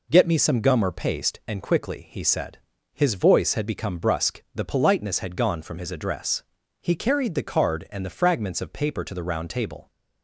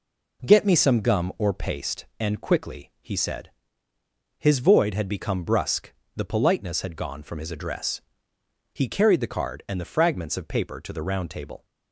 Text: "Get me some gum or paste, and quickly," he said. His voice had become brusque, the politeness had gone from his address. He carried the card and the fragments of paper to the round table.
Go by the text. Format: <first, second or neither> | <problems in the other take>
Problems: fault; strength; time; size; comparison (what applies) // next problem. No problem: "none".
first | says "void" for "voice"; at 4.5 s